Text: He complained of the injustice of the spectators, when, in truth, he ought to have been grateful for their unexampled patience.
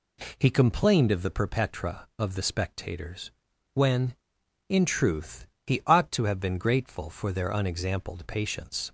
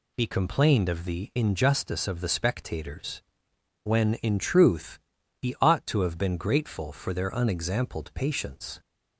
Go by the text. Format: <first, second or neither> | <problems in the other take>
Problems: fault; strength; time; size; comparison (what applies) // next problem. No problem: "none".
second | says "perpetra" for "injustice"; at 1.2 s